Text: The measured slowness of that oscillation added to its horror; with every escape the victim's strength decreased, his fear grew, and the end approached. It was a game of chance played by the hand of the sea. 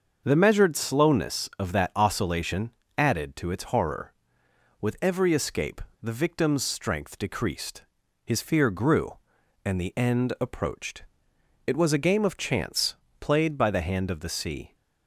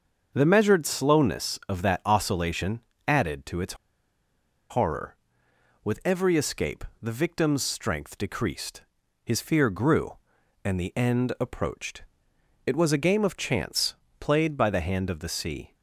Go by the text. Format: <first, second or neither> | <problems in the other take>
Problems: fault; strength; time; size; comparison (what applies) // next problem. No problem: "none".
first | starts louder than the rest; until 1.3 s; 6.5 dB; also in the first // pauses between "oscillation" and "added"; slight; at 2.7 s; 0.28 s long; slight in the first // pauses between "its" and "horror"; noticeable; at 3.7 s; 0.95 s long // pauses between "escape" and "the"; slight; at 6.8 s; 0.18 s long; slight in the first // pauses between "chance" and "played"; slight; at 13.9 s; 0.24 s long; slight in the first